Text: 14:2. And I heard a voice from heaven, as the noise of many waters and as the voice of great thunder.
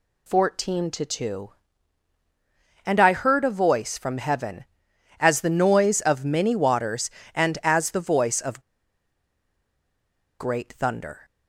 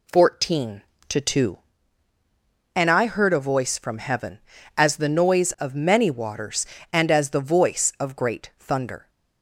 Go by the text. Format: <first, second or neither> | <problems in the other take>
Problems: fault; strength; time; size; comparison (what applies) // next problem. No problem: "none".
second | pauses between "of" and "great"; strong; at 8.6 s; 1.7 s long